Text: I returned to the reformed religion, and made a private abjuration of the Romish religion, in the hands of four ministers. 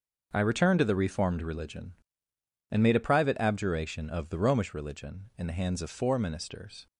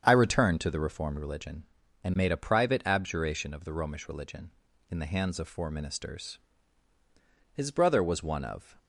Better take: first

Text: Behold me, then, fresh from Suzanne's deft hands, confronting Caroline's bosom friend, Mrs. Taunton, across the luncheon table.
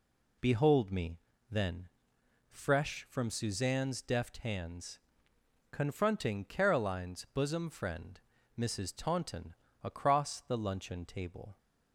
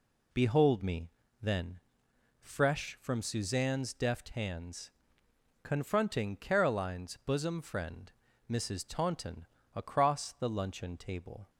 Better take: neither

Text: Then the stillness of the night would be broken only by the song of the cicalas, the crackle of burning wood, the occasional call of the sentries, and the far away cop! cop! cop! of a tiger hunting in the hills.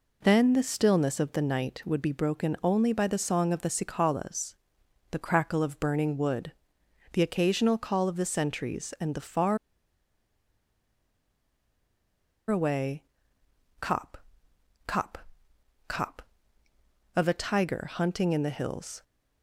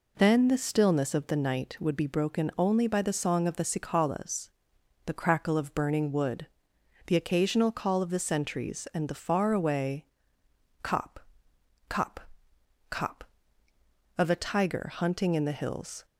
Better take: second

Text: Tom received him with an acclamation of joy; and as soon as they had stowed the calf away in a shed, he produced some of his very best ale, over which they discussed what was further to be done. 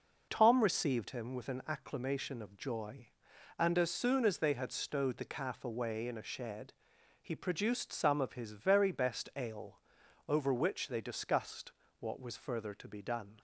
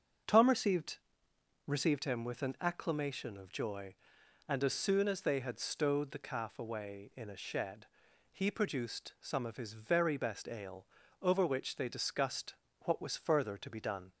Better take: first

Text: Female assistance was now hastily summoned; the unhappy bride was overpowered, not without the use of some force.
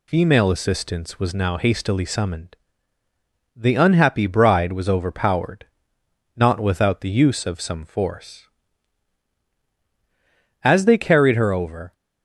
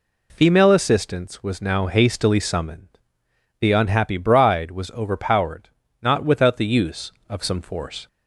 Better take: second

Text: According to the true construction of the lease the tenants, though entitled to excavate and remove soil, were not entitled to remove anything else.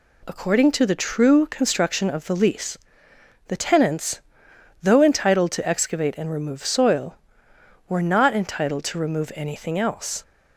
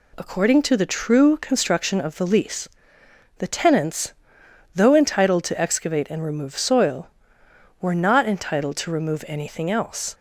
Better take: neither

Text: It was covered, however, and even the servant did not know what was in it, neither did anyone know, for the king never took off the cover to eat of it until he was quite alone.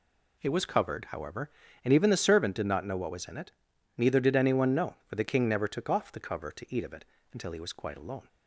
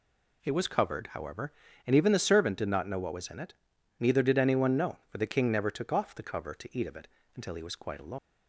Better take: first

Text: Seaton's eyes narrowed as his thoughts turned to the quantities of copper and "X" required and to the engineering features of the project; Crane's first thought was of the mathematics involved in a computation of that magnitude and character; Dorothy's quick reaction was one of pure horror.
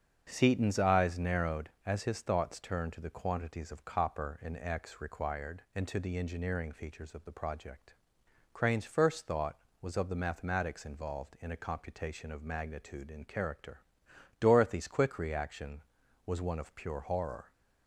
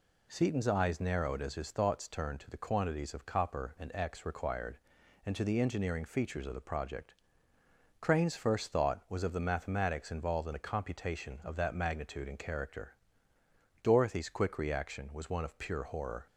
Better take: second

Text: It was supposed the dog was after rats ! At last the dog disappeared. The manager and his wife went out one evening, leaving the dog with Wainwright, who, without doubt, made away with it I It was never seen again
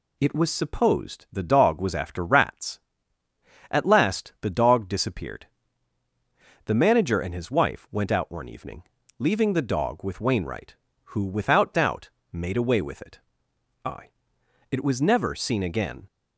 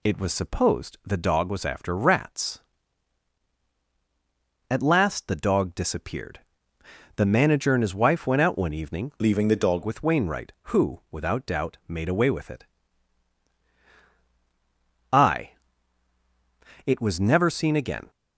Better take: first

